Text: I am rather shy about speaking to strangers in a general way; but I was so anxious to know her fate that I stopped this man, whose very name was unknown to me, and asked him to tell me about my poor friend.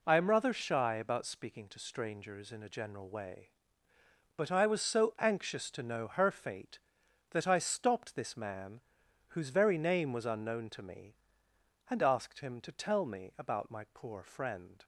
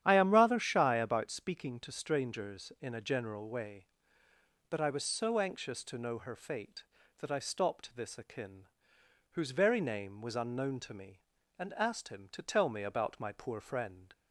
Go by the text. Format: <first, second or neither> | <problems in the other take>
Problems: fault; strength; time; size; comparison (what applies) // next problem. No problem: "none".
first | starts louder than the rest; strong; until 1.0 s; 10 dB // says "akin" for "man"; at 8.1 s